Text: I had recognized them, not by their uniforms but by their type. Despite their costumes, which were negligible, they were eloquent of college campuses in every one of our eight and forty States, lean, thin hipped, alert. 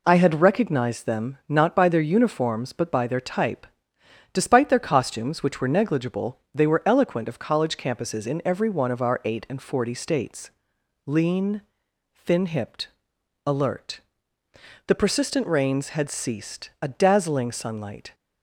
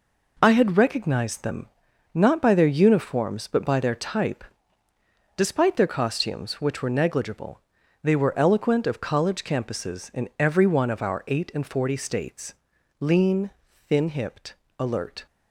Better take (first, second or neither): second